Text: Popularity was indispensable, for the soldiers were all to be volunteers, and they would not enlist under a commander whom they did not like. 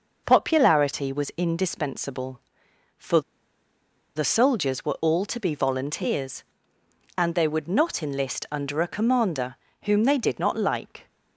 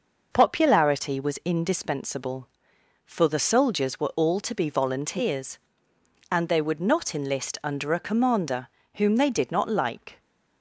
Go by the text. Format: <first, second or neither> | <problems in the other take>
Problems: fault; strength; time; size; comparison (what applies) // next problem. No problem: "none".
second | pauses between "for" and "the"; noticeable; at 3.2 s; 0.95 s long // pauses between "commander" and "whom"; slight; at 9.5 s; 0.30 s long; slight in the second